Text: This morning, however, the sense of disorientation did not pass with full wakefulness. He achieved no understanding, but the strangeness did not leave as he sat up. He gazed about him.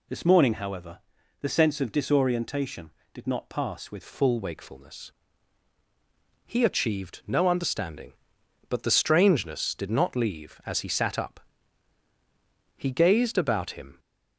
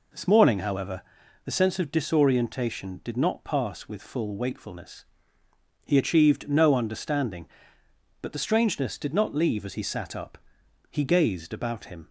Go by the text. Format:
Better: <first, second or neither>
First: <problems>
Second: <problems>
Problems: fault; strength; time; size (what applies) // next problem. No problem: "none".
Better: second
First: changes voice at "full"; from 4.0 s on; 9.9 s long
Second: none